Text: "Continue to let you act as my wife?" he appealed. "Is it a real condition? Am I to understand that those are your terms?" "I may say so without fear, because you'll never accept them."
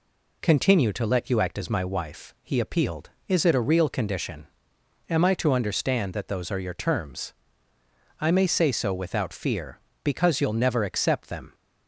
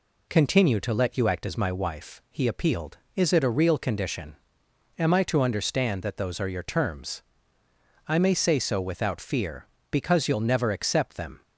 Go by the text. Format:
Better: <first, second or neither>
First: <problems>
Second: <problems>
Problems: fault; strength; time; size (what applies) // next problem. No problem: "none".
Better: neither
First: none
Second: none